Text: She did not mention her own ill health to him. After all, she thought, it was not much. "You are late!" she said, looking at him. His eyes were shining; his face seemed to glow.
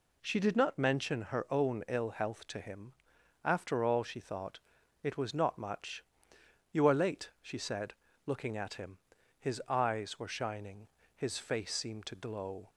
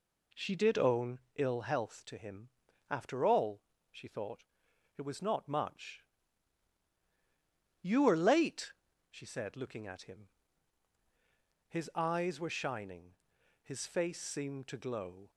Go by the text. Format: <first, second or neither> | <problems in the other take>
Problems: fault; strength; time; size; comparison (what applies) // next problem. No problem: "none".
first | skips "not mention her"; at 0.7 s // pauses between "own" and "ill"; slight; at 1.1 s; 0.18 s long